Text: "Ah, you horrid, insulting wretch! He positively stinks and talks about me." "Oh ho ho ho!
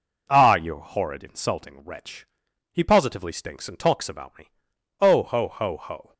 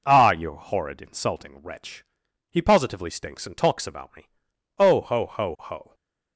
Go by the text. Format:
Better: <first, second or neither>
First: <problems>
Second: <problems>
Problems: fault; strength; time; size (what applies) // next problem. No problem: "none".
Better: neither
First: none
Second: none